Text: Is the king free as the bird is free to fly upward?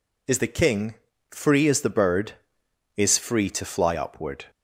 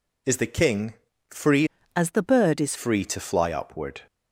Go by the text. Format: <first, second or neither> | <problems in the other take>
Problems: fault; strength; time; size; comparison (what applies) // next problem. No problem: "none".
first | pauses between "king" and "free"; at 0.9 s; 0.38 s long; also in the first // changes voice from "as" to "is"; from 1.9 to 2.7 s; 0.8 s long